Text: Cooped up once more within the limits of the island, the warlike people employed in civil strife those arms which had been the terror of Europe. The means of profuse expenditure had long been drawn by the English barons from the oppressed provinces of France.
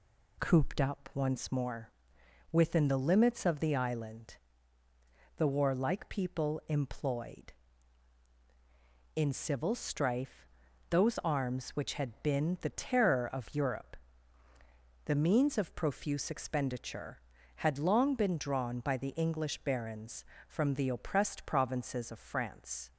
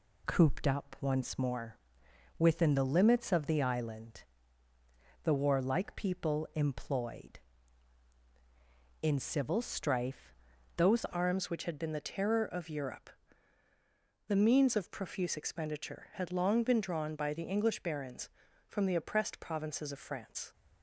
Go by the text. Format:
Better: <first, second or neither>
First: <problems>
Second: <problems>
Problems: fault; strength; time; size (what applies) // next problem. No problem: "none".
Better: first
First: pauses between "more" and "within"; noticeable; at 1.9 s; 0.62 s long // pauses between "strife" and "those"; at 10.4 s; 0.44 s long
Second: pauses between "more" and "within"; noticeable; at 1.7 s; 0.62 s long // pauses between "strife" and "those"; at 10.3 s; 0.44 s long // changes voice at "arms"; from 11.0 s on; 9.5 s long